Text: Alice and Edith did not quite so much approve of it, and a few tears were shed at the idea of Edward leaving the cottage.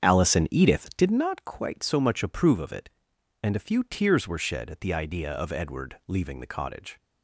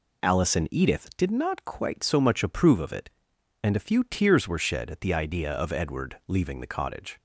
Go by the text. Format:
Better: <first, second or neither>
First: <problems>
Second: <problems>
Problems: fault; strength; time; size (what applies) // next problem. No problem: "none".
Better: second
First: starts louder than the rest; strong; until 1.3 s; 8 dB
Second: none